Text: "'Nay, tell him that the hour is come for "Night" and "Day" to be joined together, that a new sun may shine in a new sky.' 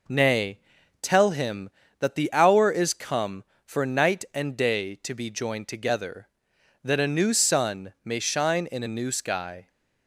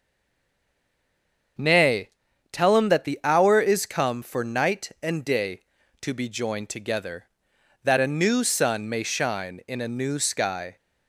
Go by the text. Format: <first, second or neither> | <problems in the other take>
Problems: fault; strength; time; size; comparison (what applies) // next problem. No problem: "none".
first | stays silent before the first word; noticeable; until 1.5 s; 1.5 s long // starts louder than the rest; until 3.0 s; 7 dB